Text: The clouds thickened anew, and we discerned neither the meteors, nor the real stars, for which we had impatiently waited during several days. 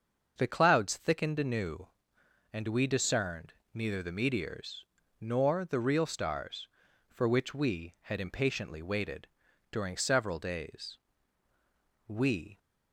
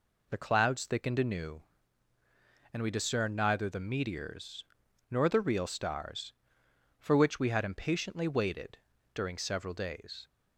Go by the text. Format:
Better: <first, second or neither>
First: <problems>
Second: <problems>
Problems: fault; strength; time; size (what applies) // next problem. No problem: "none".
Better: second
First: starts louder than the rest; until 1.3 s; 6.5 dB // pauses between "discerned" and "neither"; slight; at 3.5 s; 0.18 s long // pauses between "waited" and "during"; at 9.2 s; 0.42 s long // goes on to say "We"; from 12.0 s on; 0.52 s long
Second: pauses between "waited" and "during"; slight; at 8.7 s; 0.36 s long